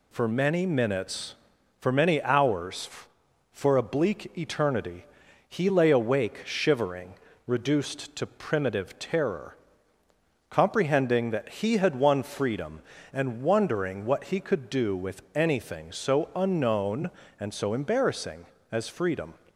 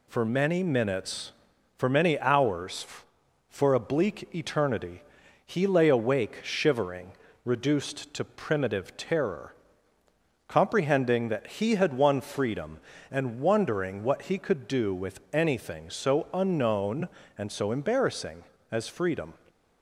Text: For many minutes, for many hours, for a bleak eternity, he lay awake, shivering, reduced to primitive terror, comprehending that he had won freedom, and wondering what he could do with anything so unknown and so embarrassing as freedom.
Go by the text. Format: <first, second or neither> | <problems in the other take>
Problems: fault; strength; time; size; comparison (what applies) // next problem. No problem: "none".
neither | none